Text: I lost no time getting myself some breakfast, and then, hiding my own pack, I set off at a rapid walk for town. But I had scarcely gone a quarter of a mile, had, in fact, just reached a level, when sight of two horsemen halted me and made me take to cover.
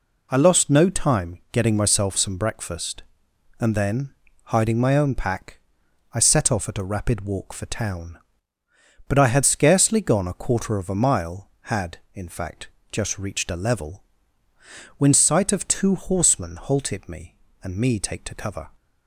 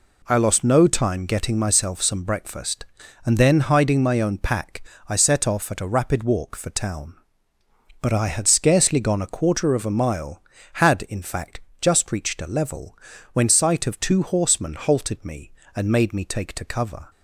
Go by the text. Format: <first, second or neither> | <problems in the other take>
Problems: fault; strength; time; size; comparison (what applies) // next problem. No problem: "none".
second | skips "made"; at 17.7 s